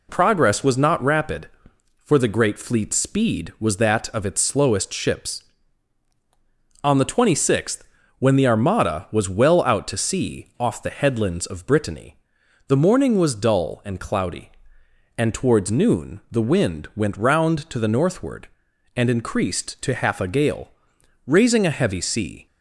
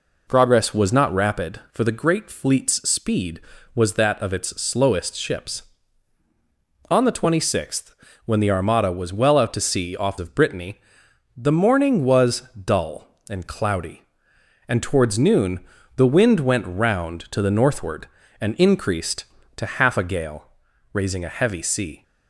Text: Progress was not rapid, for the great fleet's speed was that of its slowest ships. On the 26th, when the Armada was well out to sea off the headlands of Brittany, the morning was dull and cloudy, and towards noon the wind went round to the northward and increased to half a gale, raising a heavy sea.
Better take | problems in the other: first | skips "the headlands"; at 10.1 s // pauses between "was" and "dull"; slight; at 12.4 s; 0.20 s long // pauses between "noon" and "the"; at 15.5 s; 0.38 s long

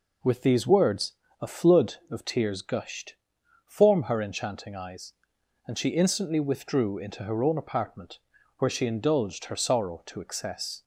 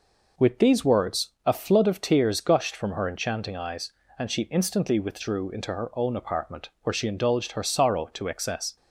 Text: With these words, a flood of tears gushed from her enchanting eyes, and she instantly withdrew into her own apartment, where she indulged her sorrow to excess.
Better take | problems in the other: second | says "form" for "from"; at 3.6 s

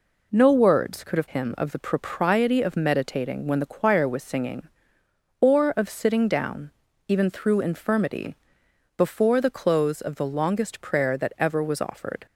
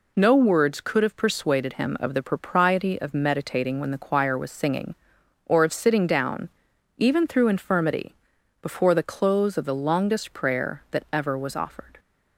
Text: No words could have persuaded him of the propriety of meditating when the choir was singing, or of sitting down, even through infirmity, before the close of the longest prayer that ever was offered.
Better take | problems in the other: second | skips "persuaded"; at 1.2 s

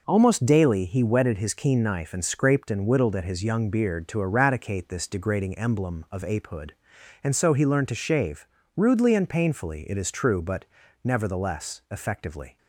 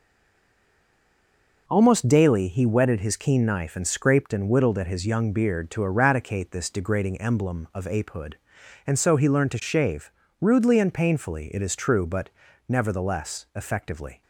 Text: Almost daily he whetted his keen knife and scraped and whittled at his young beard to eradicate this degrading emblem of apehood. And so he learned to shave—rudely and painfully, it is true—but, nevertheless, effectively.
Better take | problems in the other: first | stays silent before the first word; noticeable; until 1.6 s; 1.6 s long

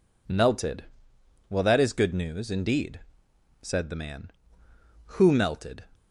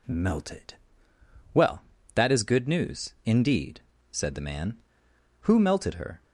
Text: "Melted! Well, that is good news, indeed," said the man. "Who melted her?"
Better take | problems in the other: second | stops before "her"; at 5.9 s

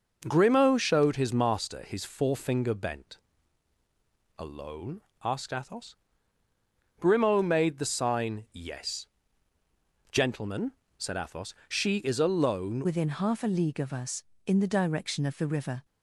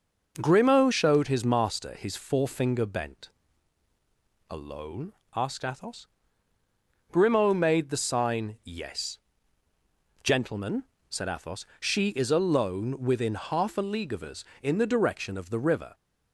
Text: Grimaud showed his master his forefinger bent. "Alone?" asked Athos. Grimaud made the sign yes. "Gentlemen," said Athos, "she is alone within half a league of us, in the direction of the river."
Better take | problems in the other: second | changes voice at "within"; from 12.8 s on; 3.0 s long

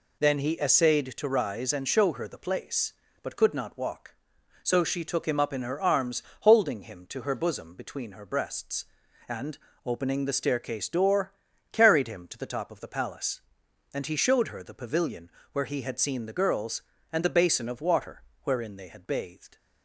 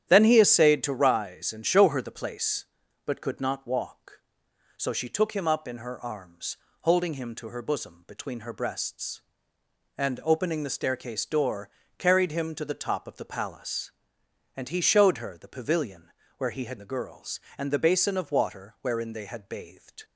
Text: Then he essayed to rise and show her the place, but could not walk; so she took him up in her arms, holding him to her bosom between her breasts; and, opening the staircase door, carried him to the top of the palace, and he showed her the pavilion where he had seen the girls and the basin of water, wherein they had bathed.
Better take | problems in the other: first | starts louder than the rest; strong; until 1.0 s; 10.5 dB // pauses between "pavilion" and "where"; slight; at 16.1 s; 0.28 s long; slight in the first // skips "seen"; at 16.7 s

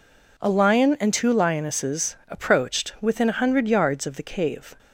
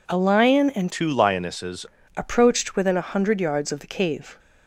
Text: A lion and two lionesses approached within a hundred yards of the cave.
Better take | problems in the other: first | changes voice from "two" to "lionesses"; from 0.9 to 1.8 s; 0.9 s long

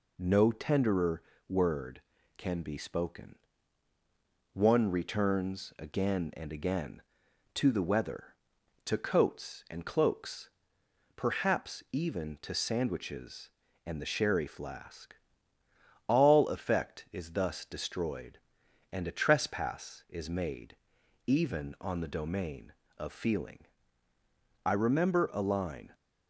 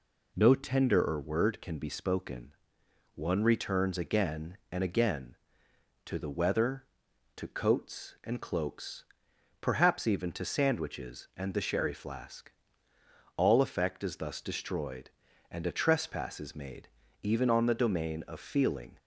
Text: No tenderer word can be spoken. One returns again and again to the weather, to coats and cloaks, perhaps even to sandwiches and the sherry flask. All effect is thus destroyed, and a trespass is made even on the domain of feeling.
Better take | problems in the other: second | pauses between "tenderer" and "word"; slight; at 1.2 s; 0.26 s long // pauses between "made" and "even"; noticeable; at 20.7 s; 0.50 s long; slight in the second // goes on to say "I remember a line"; noticeable; from 24.6 s on; 1.3 s long

